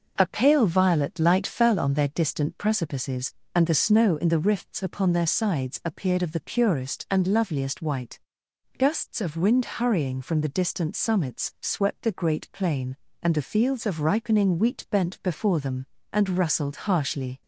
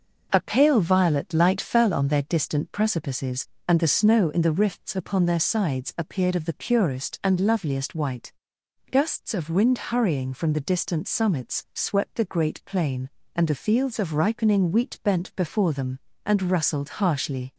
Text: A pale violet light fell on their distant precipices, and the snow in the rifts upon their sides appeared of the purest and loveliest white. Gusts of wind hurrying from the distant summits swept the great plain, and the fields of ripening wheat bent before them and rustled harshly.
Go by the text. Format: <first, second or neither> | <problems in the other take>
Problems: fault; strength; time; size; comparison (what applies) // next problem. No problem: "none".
neither | none